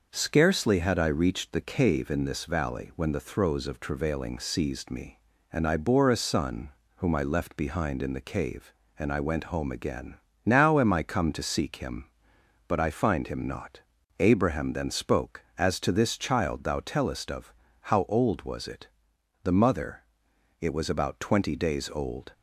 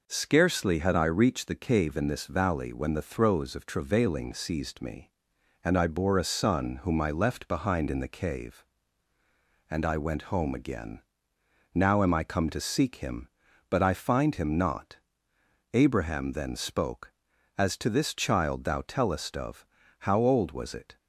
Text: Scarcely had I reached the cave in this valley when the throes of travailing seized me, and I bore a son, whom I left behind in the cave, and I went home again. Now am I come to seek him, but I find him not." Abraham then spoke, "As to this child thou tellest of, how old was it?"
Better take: second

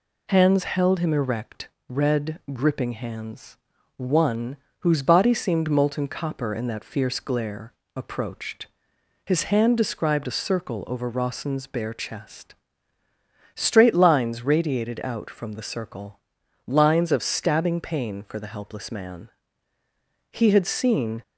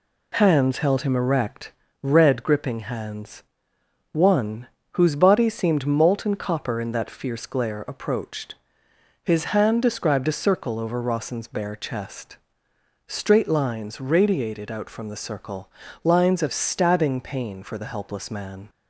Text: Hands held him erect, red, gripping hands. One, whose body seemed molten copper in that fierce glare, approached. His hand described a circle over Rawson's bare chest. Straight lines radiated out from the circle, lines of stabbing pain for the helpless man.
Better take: second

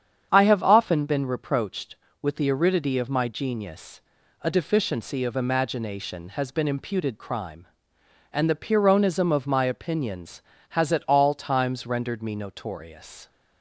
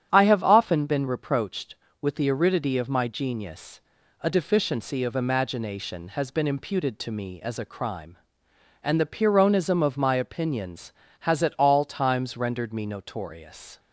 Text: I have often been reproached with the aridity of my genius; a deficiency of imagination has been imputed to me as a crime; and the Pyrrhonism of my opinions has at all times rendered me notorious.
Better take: second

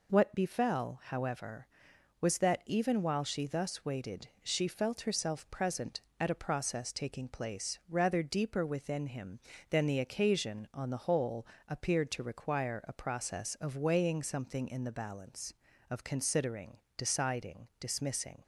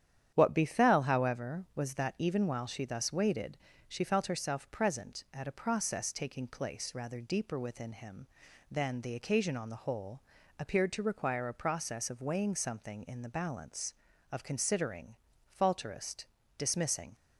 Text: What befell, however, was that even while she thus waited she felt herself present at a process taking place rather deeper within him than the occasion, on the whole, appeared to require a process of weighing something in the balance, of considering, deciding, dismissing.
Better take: first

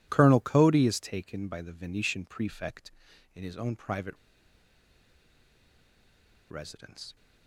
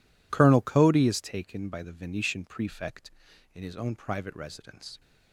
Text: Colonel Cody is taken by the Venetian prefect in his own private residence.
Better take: second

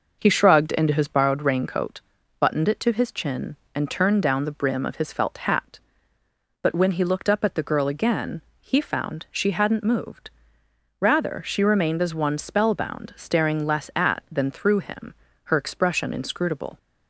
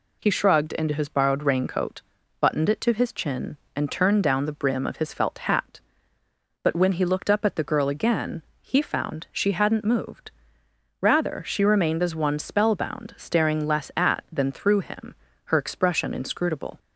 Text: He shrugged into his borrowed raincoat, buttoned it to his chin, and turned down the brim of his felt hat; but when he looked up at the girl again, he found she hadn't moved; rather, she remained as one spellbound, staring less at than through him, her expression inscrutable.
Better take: second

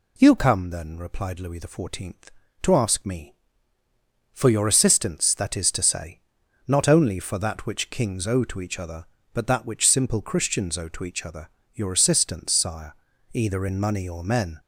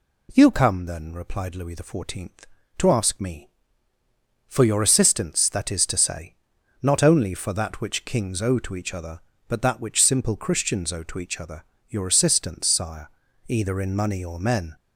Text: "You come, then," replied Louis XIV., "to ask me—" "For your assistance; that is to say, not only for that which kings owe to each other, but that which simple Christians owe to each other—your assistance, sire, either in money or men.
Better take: second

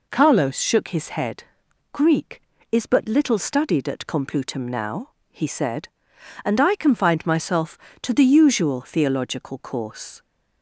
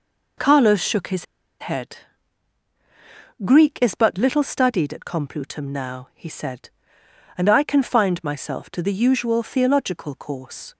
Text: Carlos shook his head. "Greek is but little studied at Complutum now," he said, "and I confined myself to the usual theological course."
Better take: first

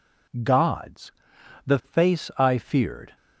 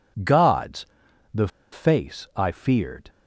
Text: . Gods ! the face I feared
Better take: first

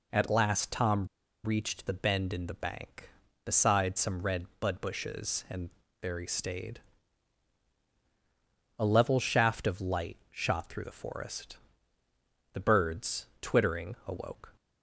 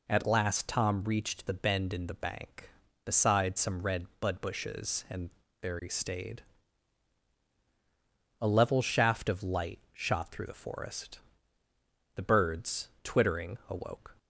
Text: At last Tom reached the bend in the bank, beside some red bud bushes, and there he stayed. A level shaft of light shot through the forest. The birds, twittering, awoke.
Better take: second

